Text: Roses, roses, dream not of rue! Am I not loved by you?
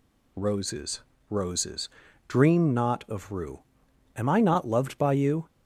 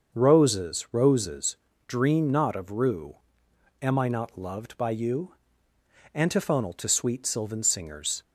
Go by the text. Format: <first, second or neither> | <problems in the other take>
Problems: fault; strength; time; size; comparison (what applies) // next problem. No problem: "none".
first | starts louder than the rest; until 1.2 s; 6.5 dB // goes on to say "Antiphonal to sweet sylvan singers"; strong; from 6.1 s on; 2.0 s long